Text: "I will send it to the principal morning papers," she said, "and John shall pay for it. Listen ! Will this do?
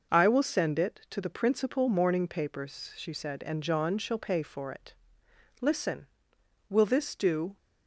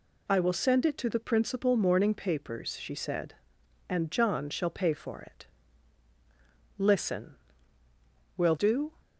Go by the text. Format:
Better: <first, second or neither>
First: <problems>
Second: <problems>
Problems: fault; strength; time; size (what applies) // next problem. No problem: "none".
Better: first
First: none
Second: skips "this"; at 8.5 s